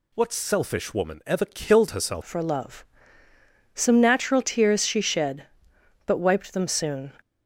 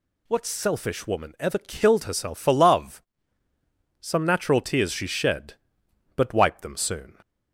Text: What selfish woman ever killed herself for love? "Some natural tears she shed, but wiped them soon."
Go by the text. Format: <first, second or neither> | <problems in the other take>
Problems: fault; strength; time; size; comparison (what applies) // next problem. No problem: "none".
second | changes voice at "for"; from 2.2 s on; 4.9 s long